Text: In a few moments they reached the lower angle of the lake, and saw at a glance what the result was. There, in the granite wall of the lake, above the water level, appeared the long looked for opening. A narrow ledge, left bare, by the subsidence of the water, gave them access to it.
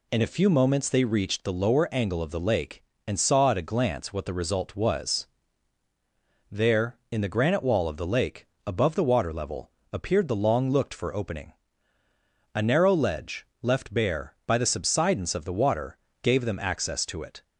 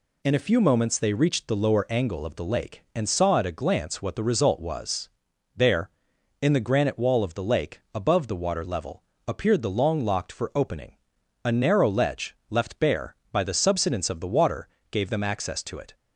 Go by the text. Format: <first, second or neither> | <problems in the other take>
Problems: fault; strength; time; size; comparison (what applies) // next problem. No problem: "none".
first | says "locked" for "looked"; at 10.0 s